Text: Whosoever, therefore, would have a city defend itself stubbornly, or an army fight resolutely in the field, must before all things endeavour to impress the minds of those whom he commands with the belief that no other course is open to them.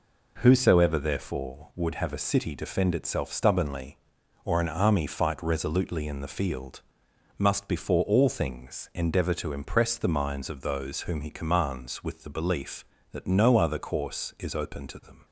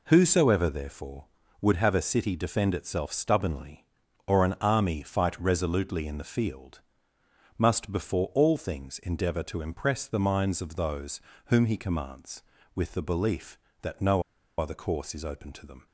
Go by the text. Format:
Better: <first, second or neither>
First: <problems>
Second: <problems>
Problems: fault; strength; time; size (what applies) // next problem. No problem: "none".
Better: first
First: none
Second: pauses between "those" and "whom"; slight; at 11.2 s; 0.24 s long // pauses between "no" and "other"; slight; at 14.2 s; 0.35 s long